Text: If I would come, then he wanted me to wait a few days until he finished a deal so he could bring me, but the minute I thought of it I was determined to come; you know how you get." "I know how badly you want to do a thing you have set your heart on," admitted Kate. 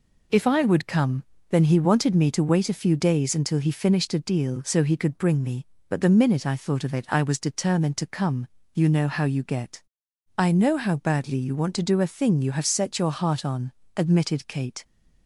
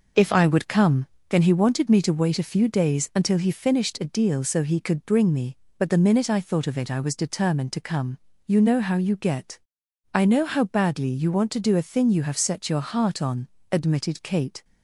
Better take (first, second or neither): first